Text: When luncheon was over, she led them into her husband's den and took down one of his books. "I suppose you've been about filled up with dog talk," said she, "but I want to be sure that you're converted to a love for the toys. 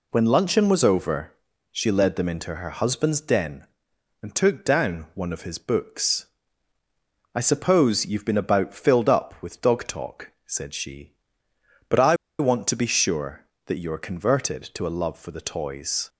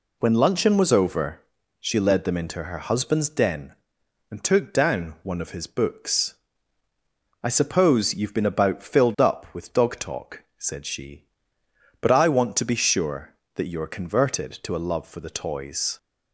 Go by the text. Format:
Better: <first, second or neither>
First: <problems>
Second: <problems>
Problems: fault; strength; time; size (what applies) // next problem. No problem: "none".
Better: second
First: pauses between "I" and "want"; slight; at 12.1 s; 0.23 s long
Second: none